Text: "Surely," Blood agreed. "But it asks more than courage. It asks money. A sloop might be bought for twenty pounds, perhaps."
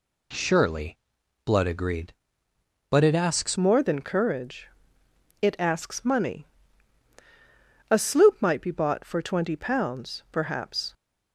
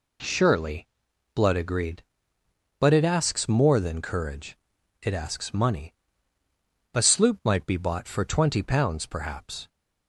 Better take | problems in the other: second | changes voice at "more"; from 3.5 s on; 7.4 s long

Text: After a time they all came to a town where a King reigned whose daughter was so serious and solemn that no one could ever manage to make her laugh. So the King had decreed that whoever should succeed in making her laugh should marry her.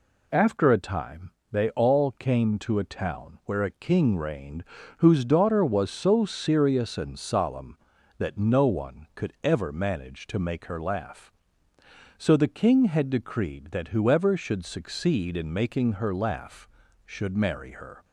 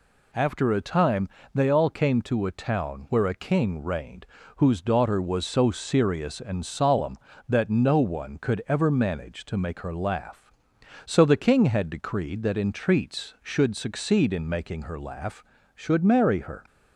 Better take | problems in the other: first | pauses between "time" and "they"; slight; at 1.2 s; 0.28 s long; slight in the first // pauses between "reigned" and "whose"; slight; at 4.2 s; 0.32 s long; slight in the first // says "entreats" for "whoever"; at 12.5 s

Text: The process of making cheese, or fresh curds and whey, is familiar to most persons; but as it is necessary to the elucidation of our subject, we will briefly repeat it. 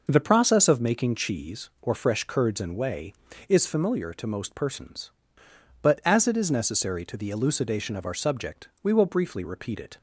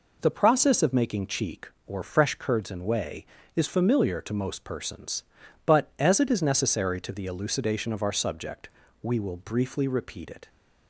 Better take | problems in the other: first | says "cheek" for "cheese"; at 1.2 s

